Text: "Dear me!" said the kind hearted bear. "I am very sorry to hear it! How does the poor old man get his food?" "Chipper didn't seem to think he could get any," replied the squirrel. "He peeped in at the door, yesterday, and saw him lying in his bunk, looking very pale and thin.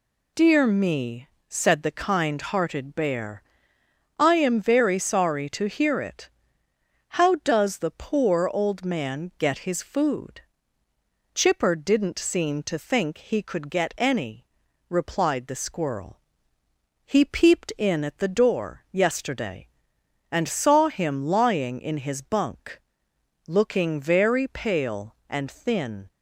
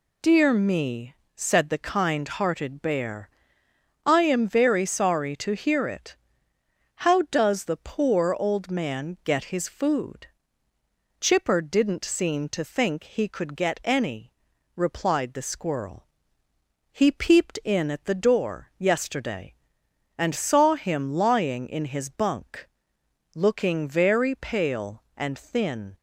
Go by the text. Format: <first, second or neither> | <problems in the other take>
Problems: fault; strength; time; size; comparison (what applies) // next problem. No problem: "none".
neither | none